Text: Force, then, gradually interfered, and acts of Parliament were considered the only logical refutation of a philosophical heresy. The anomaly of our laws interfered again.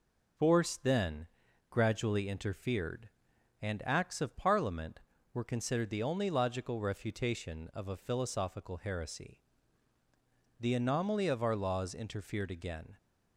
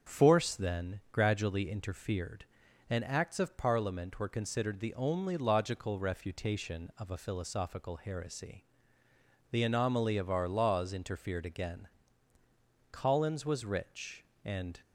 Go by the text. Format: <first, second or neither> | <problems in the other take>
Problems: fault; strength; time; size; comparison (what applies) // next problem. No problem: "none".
first | starts louder than the rest; until 1.1 s; 7 dB // goes on to say "Collins was rich and"; strong; from 12.9 s on; 1.8 s long